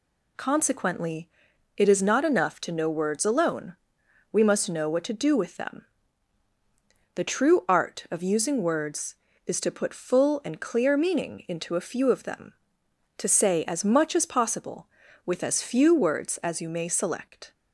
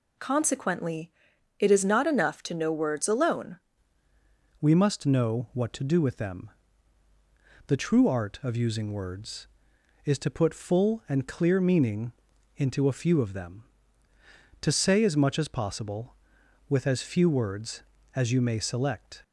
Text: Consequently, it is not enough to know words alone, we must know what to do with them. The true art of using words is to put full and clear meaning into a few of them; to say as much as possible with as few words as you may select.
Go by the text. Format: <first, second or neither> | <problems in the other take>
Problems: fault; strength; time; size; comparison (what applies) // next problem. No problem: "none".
first | changes voice at "we"; from 4.6 s on; 14.6 s long // pauses between "meaning" and "into"; noticeable; at 12.1 s; 0.46 s long